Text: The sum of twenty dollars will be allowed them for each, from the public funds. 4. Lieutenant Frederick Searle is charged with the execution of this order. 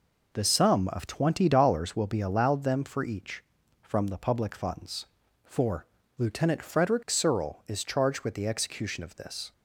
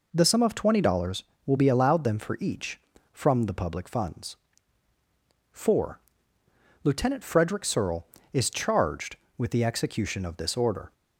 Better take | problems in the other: second | stops before "order"; at 9.5 s

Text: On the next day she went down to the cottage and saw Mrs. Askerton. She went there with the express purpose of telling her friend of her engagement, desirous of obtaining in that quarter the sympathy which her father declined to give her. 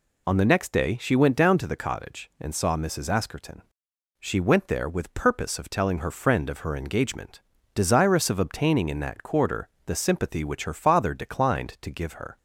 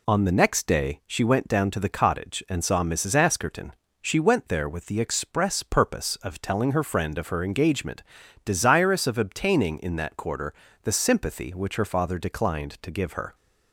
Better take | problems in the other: second | skips "the express"; at 5.1 s // pauses between "quarter" and "the"; slight; at 9.6 s; 0.20 s long; slight in the second

